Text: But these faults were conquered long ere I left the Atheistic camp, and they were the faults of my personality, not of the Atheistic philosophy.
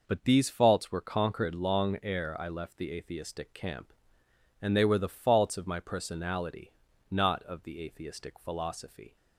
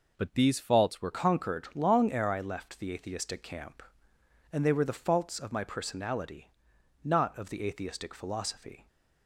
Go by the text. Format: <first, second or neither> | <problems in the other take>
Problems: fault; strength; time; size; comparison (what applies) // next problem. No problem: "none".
first | changes voice at "conquered"; from 1.1 s on; 7.7 s long